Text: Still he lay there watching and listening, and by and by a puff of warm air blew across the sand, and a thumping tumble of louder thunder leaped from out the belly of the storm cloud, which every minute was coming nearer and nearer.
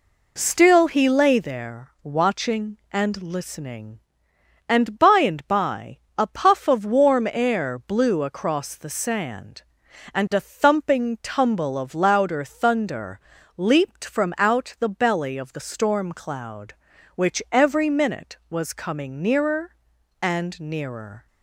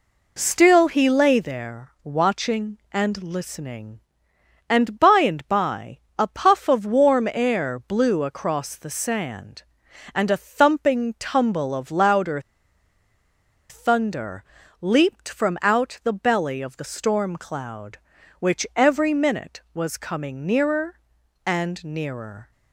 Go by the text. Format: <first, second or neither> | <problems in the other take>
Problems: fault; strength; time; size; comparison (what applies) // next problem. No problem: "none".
first | pauses between "by" and "a"; slight; at 5.9 s; 0.22 s long; slight in the first // pauses between "louder" and "thunder"; strong; at 12.3 s; 1.3 s long // pauses between "thunder" and "leaped"; at 14.4 s; 0.38 s long; also in the first